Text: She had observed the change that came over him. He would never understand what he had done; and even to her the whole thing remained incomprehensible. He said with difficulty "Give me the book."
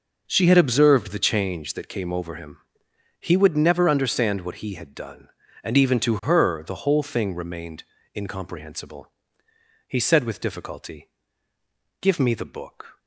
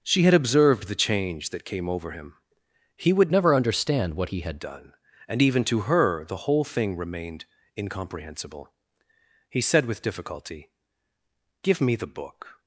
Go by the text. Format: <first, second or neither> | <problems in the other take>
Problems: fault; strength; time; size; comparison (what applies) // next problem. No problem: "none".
first | changes voice from "never" to "had"; from 3.3 to 4.5 s; 1.2 s long // pauses between "remained" and "incomprehensible"; slight; at 7.4 s; 0.32 s long; slight in the first // pauses between "difficulty" and "Give"; noticeable; at 10.6 s; 0.94 s long; noticeable in the first